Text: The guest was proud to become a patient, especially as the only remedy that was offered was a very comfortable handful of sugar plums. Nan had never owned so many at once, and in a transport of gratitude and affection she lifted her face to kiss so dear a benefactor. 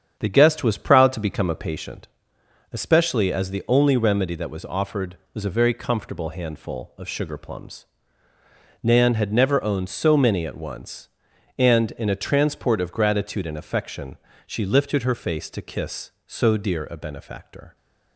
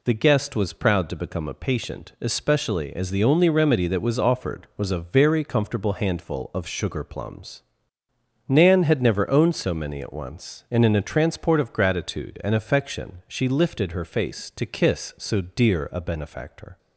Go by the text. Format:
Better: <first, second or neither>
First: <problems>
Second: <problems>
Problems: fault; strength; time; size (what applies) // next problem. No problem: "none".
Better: second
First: starts louder than the rest; strong; until 1.8 s; 8.5 dB // pauses between "affection" and "she"; slight; at 14.1 s; 0.28 s long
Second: none